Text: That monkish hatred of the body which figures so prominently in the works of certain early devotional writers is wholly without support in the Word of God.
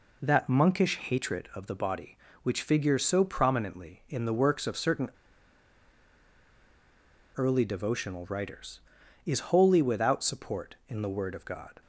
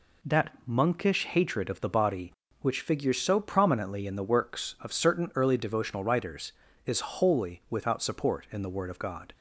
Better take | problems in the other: second | pauses between "certain" and "early"; strong; at 5.0 s; 2.2 s long

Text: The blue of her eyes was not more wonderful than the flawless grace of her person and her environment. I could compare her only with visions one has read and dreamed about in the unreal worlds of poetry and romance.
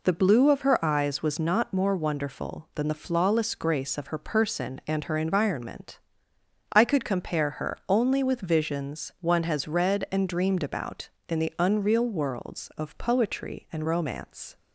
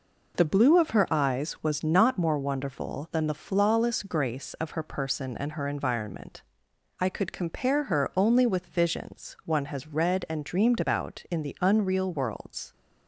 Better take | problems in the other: first | stops before "of poetry and romance"; at 12.7 s

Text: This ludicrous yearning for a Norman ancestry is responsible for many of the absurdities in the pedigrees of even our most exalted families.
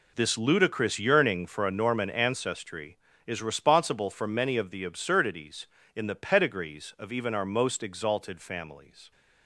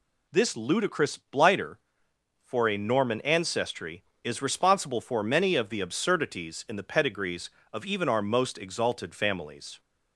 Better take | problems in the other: first | says "blighter" for "yearning"; at 1.1 s

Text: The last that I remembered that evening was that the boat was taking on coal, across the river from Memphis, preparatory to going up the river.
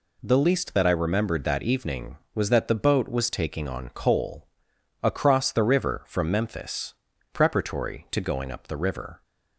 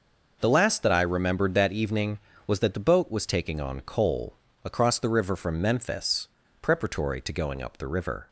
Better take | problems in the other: second | says "least" for "last"; at 0.3 s

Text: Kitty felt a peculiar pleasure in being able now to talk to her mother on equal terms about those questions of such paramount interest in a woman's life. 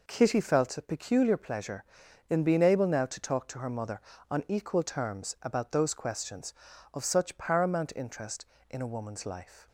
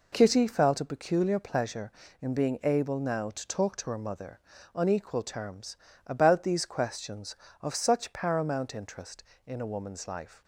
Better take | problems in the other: first | pauses between "terms" and "about"; slight; at 5.7 s; 0.30 s long // says "these" for "those"; at 6.4 s

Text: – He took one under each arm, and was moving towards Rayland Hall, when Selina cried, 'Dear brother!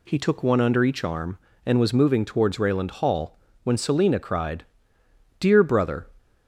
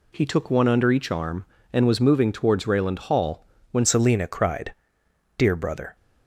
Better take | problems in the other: first | changes voice at "Selina"; from 3.8 s on; 2.1 s long

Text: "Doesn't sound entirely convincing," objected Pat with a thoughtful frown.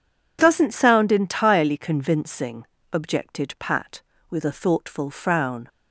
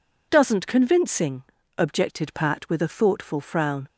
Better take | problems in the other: first | skips "sound entirely"; at 0.6 s

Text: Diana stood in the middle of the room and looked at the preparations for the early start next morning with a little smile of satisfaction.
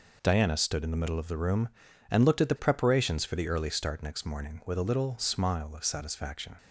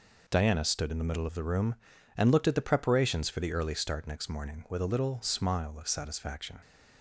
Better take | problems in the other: neither | none

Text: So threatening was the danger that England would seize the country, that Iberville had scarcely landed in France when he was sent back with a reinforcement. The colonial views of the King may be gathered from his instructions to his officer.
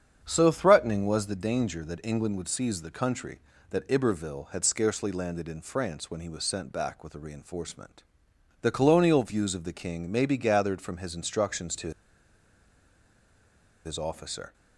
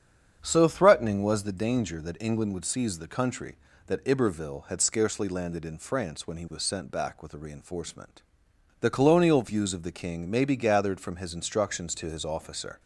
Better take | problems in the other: second | starts louder than the rest; strong; until 1.2 s; 8 dB; strong in the second // pauses between "to" and "his"; strong; at 11.9 s; 1.9 s long

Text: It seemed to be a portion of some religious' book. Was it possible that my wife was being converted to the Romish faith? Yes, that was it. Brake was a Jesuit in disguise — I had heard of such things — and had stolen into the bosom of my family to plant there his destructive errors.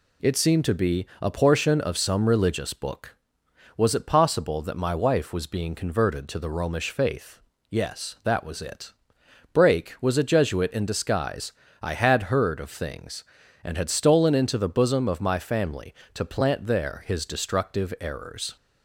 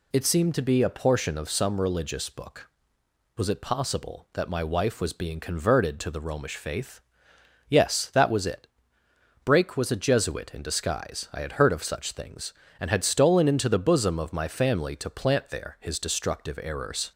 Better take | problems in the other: second | pauses between "be" and "a"; slight; at 1.0 s; 0.16 s long // skips "such"; at 12.6 s

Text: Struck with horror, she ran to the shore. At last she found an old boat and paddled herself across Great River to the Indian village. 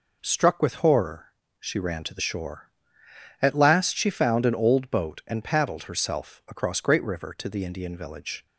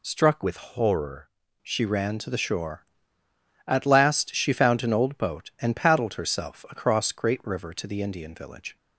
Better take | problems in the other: first | changes voice from "with" to "horror"; from 0.4 to 1.2 s; 0.8 s long

